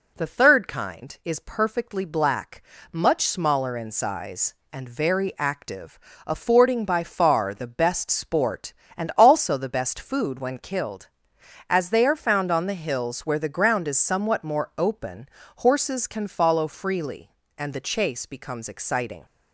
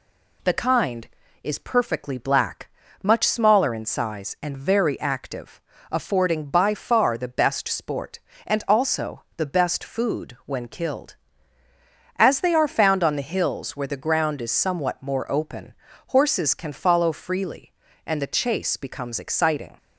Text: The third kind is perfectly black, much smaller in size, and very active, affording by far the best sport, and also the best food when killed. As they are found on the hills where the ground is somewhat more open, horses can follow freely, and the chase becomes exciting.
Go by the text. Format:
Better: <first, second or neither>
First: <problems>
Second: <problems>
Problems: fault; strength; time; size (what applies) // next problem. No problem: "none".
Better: first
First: none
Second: skips "third"; at 0.5 s